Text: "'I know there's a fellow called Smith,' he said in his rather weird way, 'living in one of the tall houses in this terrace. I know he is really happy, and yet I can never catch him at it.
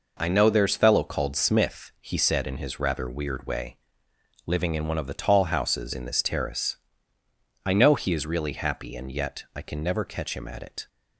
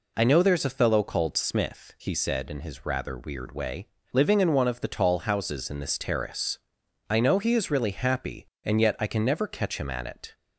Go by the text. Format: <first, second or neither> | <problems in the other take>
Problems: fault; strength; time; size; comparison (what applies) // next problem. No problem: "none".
second | skips "a"; at 0.7 s